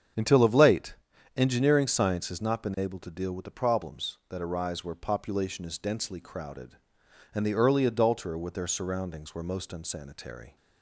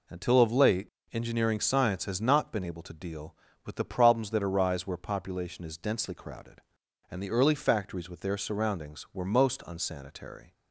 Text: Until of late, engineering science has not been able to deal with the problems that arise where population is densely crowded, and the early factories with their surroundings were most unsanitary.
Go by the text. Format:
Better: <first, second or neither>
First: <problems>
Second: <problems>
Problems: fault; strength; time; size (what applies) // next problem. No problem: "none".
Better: second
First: starts louder than the rest; strong; until 1.5 s; 8 dB // says "adulterer" for "factories"; at 7.8 s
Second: none